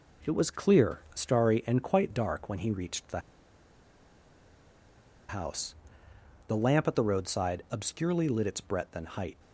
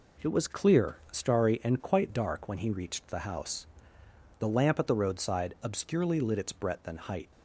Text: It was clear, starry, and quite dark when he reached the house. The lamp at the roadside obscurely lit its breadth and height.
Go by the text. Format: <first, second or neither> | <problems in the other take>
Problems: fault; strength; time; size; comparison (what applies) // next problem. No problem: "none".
second | pauses between "the" and "house"; strong; at 3.1 s; 2.0 s long